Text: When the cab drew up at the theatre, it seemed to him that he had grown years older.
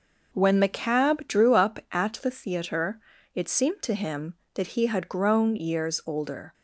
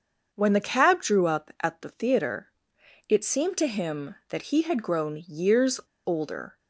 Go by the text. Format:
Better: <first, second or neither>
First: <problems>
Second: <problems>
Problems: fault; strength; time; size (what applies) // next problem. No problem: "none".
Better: first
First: none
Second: starts louder than the rest; until 1.3 s; 6.5 dB // pauses between "years" and "older"; slight; at 5.7 s; 0.28 s long